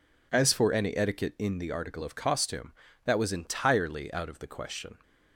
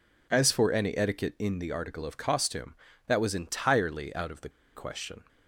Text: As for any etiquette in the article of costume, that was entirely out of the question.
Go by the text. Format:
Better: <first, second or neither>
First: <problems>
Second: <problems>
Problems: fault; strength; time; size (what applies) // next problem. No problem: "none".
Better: first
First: none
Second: pauses between "the" and "question"; slight; at 4.4 s; 0.25 s long